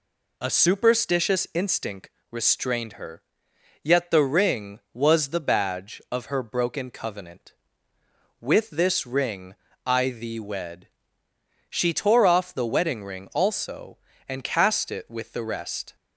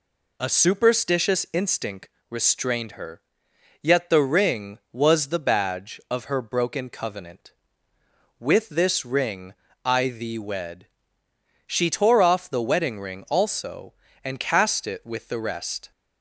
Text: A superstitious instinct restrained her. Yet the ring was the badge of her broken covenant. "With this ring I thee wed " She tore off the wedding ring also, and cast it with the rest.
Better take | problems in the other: neither | pauses between "instinct" and "restrained"; slight; the same in both // pauses between "ring" and "I"; slight; the same in both

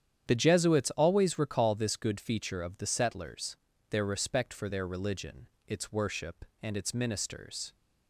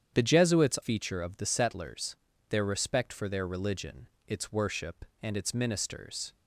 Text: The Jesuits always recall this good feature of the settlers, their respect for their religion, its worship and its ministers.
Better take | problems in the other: first | starts louder than the rest; strong; until 1.2 s; 8.5 dB; strong in the first // skips "always recall this good"; at 0.7 s

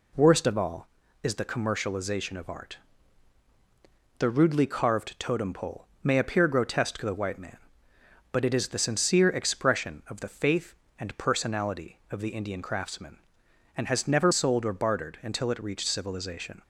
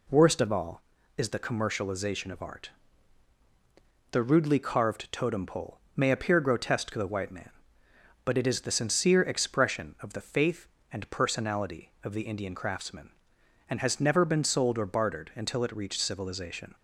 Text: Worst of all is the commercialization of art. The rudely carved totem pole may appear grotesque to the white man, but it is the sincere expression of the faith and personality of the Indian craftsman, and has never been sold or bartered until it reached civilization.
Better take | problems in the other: second | pauses between "pole" and "may"; slight; at 5.8 s; 0.18 s long; slight in the second // skips "been"; at 14.3 s

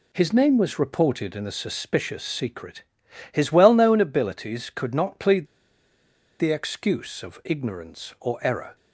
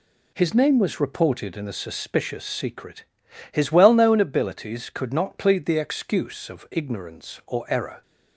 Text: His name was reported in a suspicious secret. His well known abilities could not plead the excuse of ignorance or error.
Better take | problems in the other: second | pauses between "plead" and "the"; noticeable; at 5.4 s; 0.92 s long

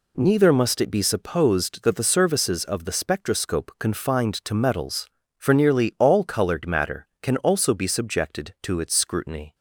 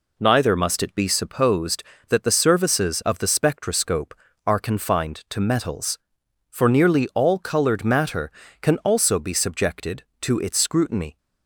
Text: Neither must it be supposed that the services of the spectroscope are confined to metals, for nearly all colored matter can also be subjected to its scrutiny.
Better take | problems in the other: second | skips "are"; at 3.7 s

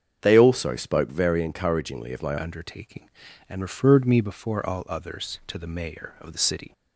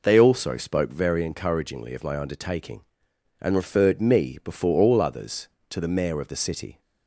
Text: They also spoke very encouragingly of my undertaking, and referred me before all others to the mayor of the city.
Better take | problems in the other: second | starts louder than the rest; strong; until 1.2 s; 7 dB // changes voice at "undertaking"; from 2.4 s on; 4.3 s long

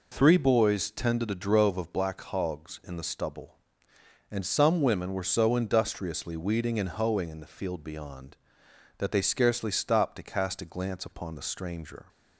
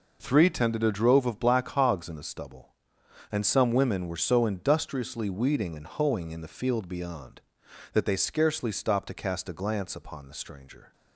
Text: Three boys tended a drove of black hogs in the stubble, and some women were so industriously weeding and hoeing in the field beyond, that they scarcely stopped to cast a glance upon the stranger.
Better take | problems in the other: first | skips "boys"; at 0.5 s

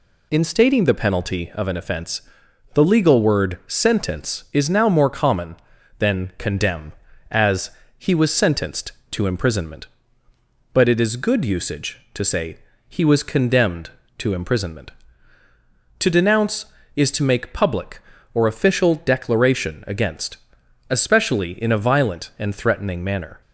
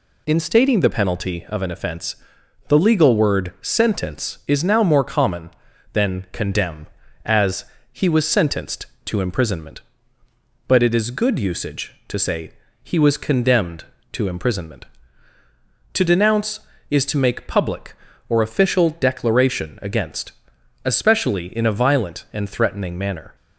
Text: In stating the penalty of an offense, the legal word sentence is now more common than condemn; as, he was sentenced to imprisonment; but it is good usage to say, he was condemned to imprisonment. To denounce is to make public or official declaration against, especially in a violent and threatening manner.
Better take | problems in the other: neither | none

